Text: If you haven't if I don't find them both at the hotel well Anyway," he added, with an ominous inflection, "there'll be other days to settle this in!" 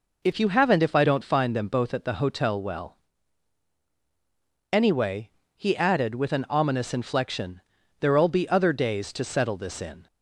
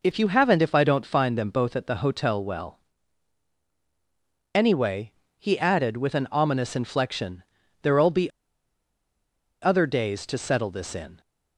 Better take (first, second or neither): first